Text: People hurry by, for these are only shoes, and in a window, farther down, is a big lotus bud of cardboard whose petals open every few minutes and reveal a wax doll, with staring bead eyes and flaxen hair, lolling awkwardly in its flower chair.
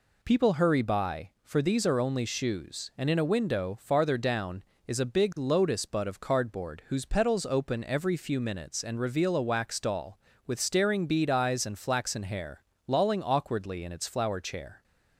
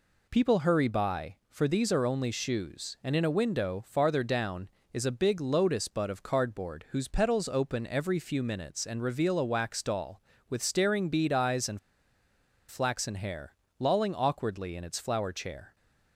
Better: first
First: none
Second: pauses between "and" and "flaxen"; noticeable; at 11.7 s; 0.91 s long

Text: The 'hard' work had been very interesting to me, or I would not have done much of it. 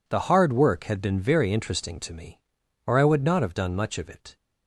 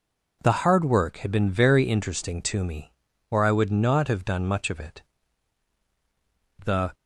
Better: first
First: none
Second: goes on to say "The"; slight; from 6.6 s on; 0.28 s long

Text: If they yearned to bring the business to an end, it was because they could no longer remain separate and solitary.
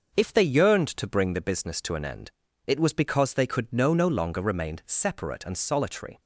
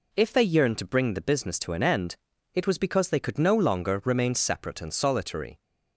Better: second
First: starts louder than the rest; until 1.2 s; 6.5 dB // says "no" twice; at 3.9 s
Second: none

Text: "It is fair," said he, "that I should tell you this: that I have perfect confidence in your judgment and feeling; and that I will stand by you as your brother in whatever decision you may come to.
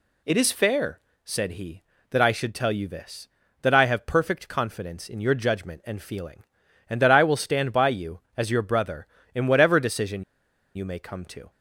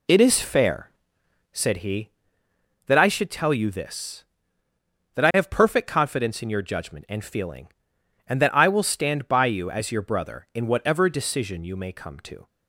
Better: second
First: pauses between "decision" and "you"; noticeable; at 10.2 s; 0.52 s long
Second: none

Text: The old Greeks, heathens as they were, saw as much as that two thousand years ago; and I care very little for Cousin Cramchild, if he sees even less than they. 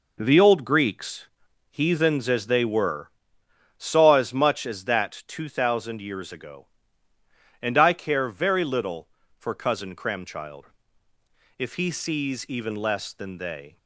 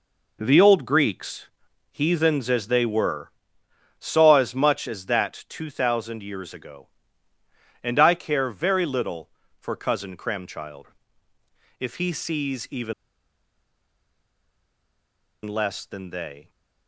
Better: first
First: none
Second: pauses between "even" and "less"; strong; at 12.9 s; 2.5 s long

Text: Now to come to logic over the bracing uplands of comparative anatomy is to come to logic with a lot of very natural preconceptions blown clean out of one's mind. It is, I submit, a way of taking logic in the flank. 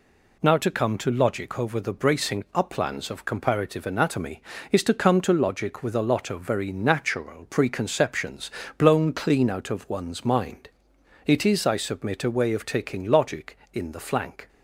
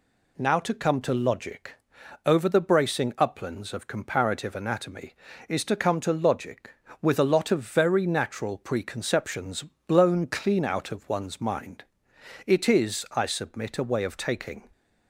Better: first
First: pauses between "preconceptions" and "blown"; slight; at 8.4 s; 0.30 s long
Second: pauses between "logic" and "over"; noticeable; at 1.7 s; 0.50 s long // pauses between "preconceptions" and "blown"; slight; at 9.6 s; 0.24 s long // stops before "logic in the flank"; at 14.7 s

